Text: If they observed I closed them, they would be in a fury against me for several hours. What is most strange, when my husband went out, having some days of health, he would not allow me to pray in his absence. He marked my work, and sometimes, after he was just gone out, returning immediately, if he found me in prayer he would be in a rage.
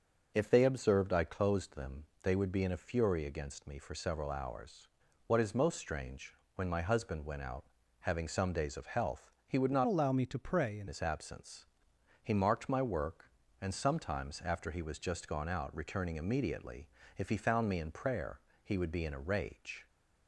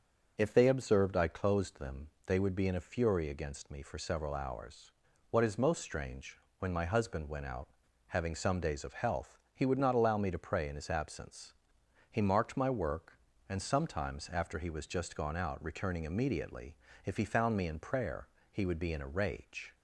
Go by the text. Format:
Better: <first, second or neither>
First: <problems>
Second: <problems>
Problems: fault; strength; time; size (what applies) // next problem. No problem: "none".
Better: second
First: starts louder than the rest; until 1.3 s; 6.5 dB // changes voice from "allow" to "in"; from 9.8 to 10.8 s; 1.0 s long // pauses between "prayer" and "he"; slight; at 18.3 s; 0.26 s long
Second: starts louder than the rest; until 1.3 s; 6.5 dB // pauses between "prayer" and "he"; slight; at 18.2 s; 0.26 s long